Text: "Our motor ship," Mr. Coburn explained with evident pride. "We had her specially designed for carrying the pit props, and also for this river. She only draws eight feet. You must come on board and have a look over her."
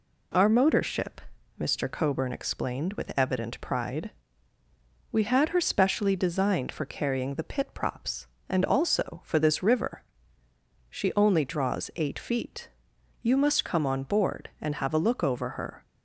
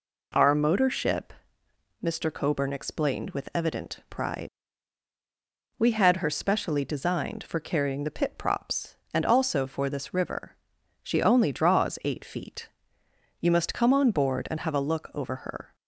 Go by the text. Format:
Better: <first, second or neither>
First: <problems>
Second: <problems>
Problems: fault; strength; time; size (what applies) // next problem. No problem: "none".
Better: neither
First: none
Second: none